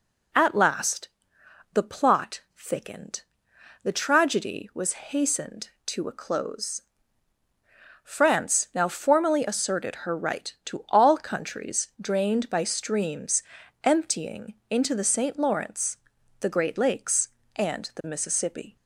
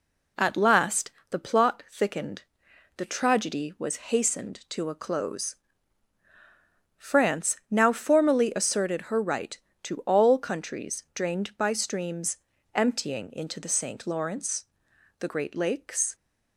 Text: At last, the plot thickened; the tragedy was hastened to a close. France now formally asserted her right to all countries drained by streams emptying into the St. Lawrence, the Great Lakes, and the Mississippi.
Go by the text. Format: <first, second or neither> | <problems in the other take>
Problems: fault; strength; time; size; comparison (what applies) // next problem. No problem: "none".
first | pauses between "streams" and "emptying"; slight; at 12.3 s; 0.36 s long; also in the first // stops before "and the Mississippi"; at 16.1 s